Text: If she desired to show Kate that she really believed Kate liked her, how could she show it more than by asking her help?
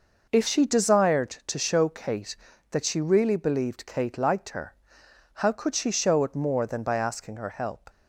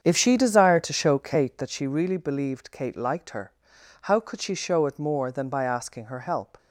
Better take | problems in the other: first | starts louder than the rest; strong; until 1.8 s; 7.5 dB

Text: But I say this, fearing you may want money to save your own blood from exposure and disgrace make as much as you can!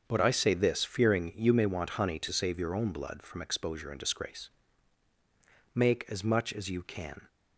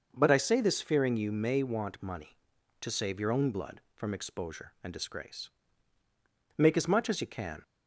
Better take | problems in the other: second | starts louder than the rest; until 1.0 s; 6.5 dB // says "honey" for "money"; at 1.9 s // pauses between "disgrace" and "make"; strong; at 4.4 s; 1.2 s long; also in the second

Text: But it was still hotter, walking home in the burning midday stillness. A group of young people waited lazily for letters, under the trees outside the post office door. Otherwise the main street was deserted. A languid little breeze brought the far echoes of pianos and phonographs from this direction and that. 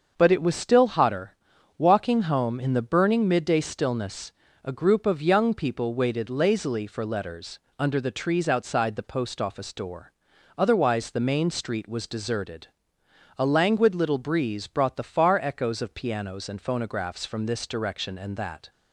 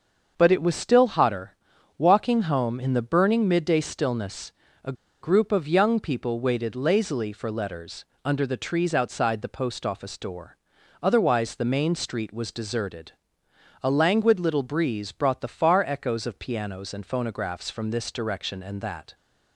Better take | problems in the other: first | starts louder than the rest; until 1.3 s; 6.5 dB; also in the first // pauses between "A" and "group"; slight; at 4.9 s; 0.28 s long

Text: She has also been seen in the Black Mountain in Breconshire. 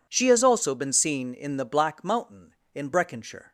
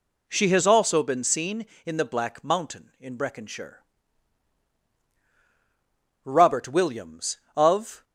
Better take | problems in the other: first | goes on to say "Robert Williams of"; strong; from 6.2 s on; 1.8 s long

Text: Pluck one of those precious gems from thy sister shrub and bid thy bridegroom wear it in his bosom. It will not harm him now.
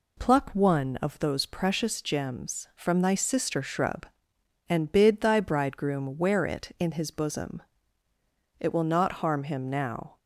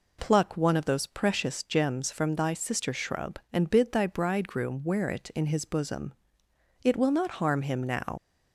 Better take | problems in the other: first | leaves "now" unfinished; at 8.1 s; 80 ms

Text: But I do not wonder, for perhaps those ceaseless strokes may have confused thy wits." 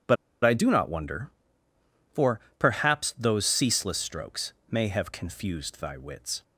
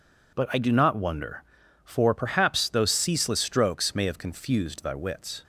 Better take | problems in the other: second | pauses between "But" and "I"; slight; at 0.1 s; 0.28 s long // pauses between "for" and "perhaps"; slight; at 2.3 s; 0.20 s long // pauses between "strokes" and "may"; slight; at 4.5 s; 0.18 s long

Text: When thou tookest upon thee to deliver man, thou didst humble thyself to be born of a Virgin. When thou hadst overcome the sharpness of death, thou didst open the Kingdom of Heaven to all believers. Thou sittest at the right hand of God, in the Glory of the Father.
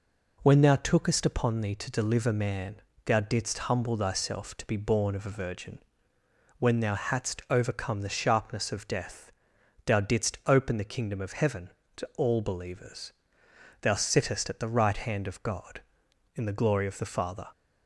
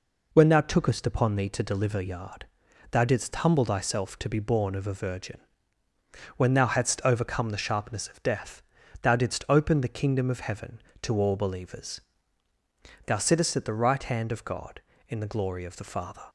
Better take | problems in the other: first | says "yard" for "man"; at 1.9 s

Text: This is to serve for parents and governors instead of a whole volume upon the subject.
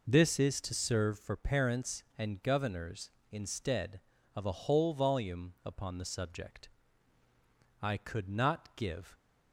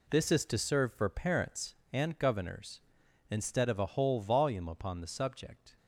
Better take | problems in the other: second | goes on to say "I could not give"; from 7.8 s on; 1.3 s long

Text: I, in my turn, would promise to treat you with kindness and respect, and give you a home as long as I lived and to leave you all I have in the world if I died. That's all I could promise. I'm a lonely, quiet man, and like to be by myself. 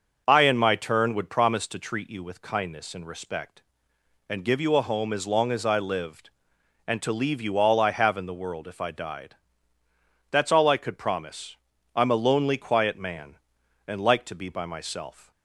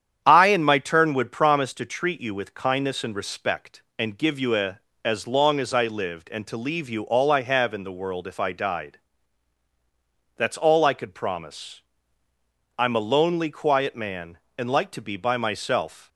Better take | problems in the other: first | starts louder than the rest; strong; until 1.2 s; 9 dB; noticeable in the first // skips "home"; at 4.9 s

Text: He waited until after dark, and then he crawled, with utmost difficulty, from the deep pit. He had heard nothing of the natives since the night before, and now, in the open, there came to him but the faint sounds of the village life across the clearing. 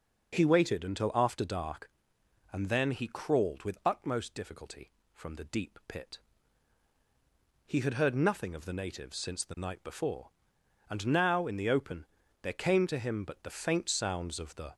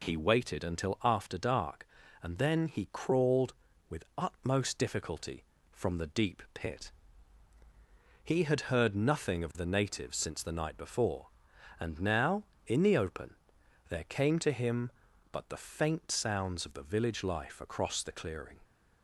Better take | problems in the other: second | stops before "village life across the clearing"; at 14.7 s

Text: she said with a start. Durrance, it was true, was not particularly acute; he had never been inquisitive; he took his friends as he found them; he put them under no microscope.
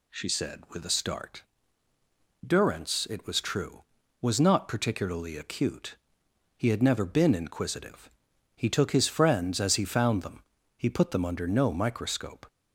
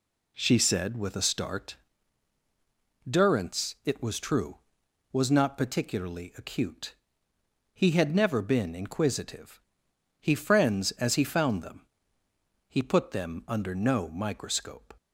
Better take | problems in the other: first | skips "took his"; at 10.3 s

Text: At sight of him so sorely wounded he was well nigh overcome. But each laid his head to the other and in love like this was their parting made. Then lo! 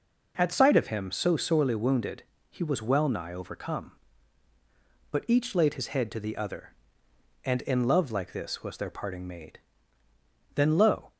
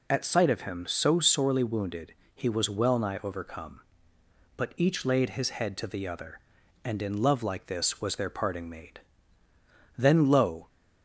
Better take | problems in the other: neither | pauses between "wounded" and "he"; slight; the same in both

